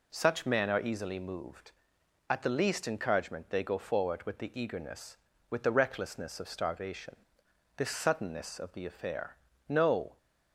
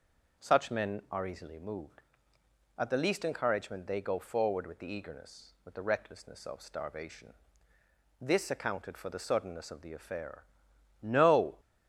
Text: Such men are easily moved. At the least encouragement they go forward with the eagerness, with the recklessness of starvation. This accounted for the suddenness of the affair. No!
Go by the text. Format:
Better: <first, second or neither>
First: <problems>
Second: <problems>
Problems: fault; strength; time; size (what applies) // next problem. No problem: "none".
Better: second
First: skips "accounted for the"; at 7.9 s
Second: none